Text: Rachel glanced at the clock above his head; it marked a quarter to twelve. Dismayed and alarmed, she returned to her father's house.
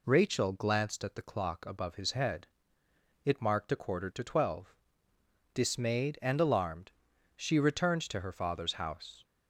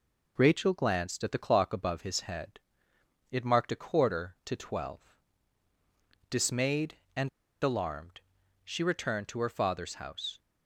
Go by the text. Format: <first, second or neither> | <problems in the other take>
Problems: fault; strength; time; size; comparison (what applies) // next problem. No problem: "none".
first | pauses between "and" and "alarmed"; slight; at 7.2 s; 0.33 s long